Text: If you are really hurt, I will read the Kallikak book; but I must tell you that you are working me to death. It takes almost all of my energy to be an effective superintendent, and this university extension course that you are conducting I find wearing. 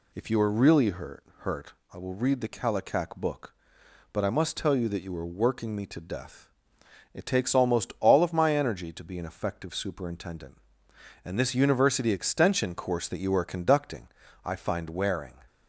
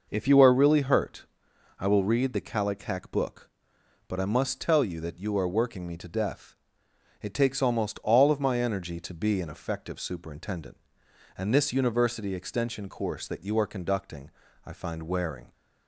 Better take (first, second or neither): second